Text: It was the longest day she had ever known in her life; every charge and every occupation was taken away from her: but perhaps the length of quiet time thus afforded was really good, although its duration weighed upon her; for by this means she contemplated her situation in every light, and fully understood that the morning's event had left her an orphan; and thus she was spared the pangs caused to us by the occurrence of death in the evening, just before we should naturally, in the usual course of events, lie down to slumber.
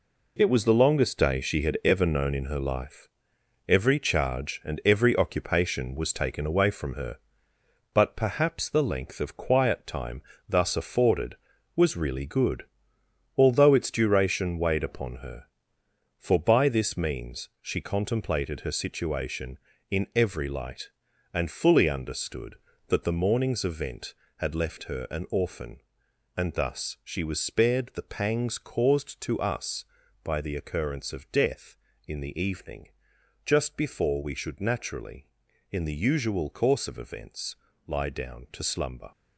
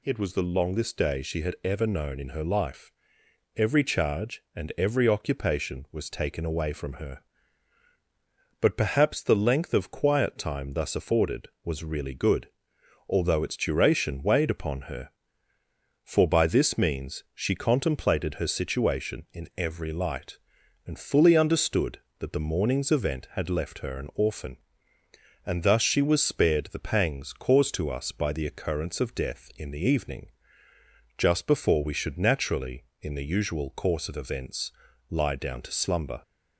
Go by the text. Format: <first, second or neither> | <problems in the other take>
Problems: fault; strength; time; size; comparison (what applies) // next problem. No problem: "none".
second | gets quieter; strong; throughout; 8 dB // pauses between "time" and "thus"; slight; at 10.2 s; 0.26 s long